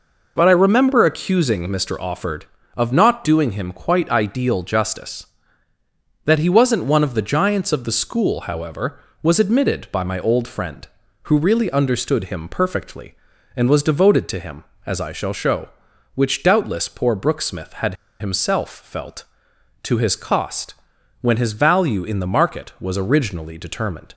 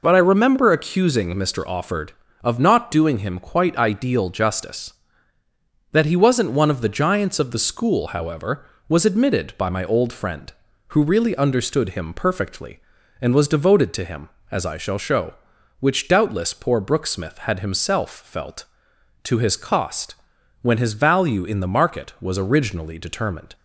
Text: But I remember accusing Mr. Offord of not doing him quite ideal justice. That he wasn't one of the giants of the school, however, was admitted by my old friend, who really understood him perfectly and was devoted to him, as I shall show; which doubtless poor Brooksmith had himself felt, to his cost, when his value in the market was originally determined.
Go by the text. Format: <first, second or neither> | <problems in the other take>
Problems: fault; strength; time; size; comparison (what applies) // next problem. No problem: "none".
second | pauses between "had" and "himself"; slight; at 17.9 s; 0.25 s long